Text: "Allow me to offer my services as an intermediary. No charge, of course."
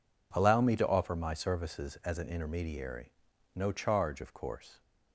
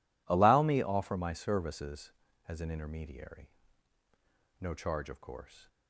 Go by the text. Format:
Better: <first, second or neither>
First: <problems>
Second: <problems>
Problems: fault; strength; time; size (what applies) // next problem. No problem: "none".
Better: first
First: none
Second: skips "to"; at 0.8 s